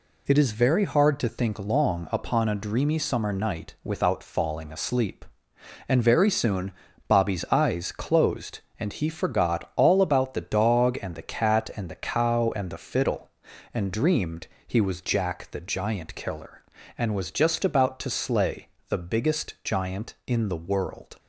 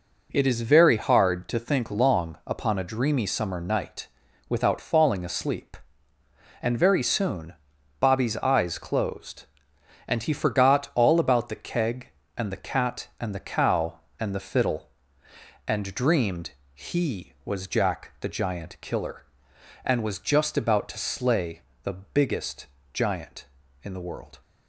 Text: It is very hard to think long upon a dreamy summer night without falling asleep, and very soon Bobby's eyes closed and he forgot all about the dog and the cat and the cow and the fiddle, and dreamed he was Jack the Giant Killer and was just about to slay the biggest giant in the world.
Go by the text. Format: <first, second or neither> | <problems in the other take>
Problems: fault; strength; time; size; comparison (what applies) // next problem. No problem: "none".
first | pauses between "night" and "without"; at 4.0 s; 0.40 s long // pauses between "soon" and "Bobby's"; noticeable; at 7.5 s; 0.46 s long; slight in the first // says "keg" for "dog"; at 11.5 s // pauses between "dreamed" and "he"; slight; at 16.5 s; 0.22 s long; slight in the first // pauses between "slay" and "the"; slight; at 21.6 s; 0.22 s long; slight in the first // pauses between "biggest" and "giant"; slight; at 22.6 s; 0.26 s long